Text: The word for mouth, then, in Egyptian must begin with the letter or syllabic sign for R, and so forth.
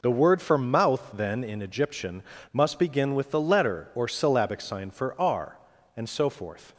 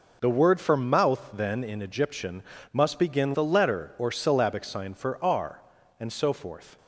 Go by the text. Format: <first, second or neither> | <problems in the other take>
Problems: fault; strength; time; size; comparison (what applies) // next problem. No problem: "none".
first | pauses between "Egyptian" and "must"; slight; at 2.4 s; 0.30 s long; slight in the first // skips "with"; at 3.3 s